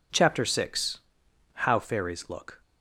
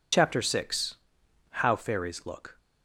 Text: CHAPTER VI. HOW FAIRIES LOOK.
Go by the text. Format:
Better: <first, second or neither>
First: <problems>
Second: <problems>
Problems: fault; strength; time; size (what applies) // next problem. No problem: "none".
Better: first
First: none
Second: loses the start of "CHAPTER"; at 0.1 s; 40 ms